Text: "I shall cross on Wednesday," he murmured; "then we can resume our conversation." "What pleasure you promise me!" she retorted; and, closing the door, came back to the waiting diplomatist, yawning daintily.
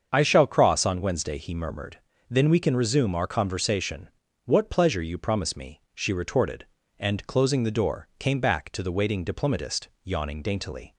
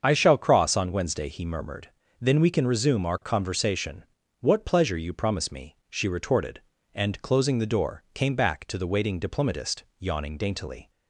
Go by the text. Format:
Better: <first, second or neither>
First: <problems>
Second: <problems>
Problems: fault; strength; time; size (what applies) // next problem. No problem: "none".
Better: neither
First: starts louder than the rest; until 1.1 s; 7 dB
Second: starts louder than the rest; until 1.0 s; 7 dB